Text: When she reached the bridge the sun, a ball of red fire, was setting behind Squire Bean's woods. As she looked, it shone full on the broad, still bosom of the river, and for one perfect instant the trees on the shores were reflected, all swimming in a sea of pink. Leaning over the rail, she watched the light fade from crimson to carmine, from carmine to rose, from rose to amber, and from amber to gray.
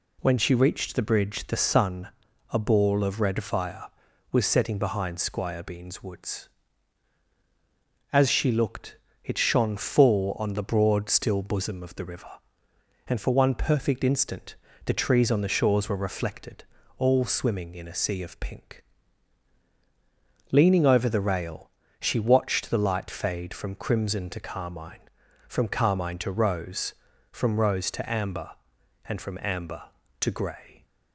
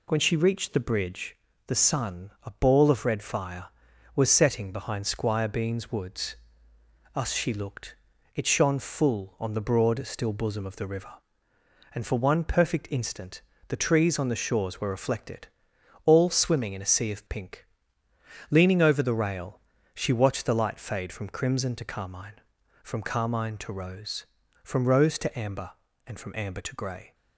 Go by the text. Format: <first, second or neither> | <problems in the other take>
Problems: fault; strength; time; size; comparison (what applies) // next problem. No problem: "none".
first | pauses between "bridge" and "the"; slight; at 1.3 s; 0.30 s long // says "Us" for "As"; at 7.1 s // pauses between "instant" and "the"; slight; at 13.4 s; 0.24 s long; slight in the first